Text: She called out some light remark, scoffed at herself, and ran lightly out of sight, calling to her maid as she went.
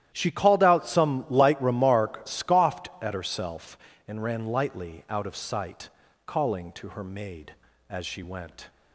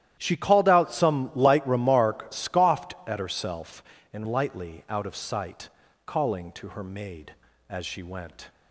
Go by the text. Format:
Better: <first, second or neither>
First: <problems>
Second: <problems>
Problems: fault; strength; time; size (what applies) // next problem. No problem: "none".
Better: first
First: starts louder than the rest; strong; until 1.1 s; 12 dB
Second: starts louder than the rest; strong; until 1.1 s; 12 dB // skips "ran"; at 4.2 s